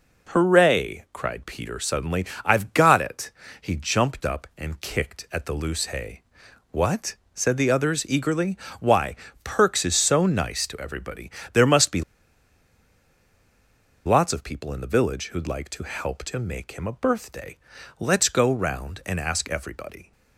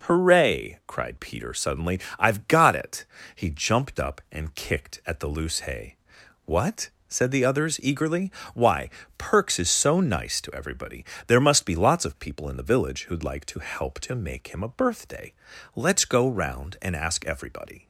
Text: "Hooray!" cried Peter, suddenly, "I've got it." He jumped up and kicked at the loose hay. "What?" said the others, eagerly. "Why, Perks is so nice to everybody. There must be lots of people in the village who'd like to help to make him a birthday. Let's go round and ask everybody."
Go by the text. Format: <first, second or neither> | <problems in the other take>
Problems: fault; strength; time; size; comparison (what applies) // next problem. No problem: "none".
second | pauses between "be" and "lots"; strong; at 12.0 s; 2.0 s long